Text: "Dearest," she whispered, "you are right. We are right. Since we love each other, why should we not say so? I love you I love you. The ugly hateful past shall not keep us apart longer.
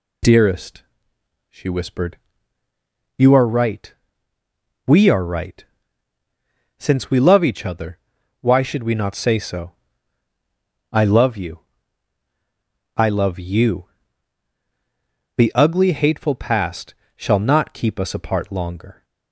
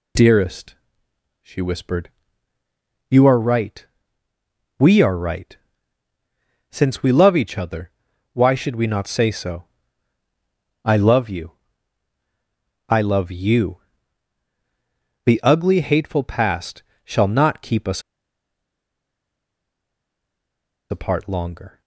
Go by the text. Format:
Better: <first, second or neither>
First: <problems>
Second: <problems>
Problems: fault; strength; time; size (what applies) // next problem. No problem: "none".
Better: first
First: pauses between "you" and "I"; strong; at 11.5 s; 1.3 s long // pauses between "past" and "shall"; slight; at 16.9 s; 0.22 s long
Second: pauses between "you" and "I"; strong; at 11.5 s; 1.3 s long // pauses between "past" and "shall"; slight; at 16.8 s; 0.22 s long // pauses between "us" and "apart"; strong; at 18.0 s; 2.8 s long